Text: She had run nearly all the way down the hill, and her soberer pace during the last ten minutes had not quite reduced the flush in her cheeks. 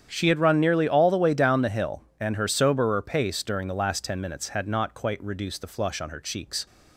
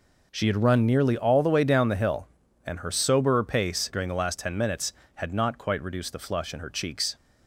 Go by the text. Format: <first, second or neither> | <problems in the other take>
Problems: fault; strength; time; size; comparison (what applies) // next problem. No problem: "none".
second | starts louder than the rest; strong; until 1.1 s; 8.5 dB // says "on" for "in"; at 6.0 s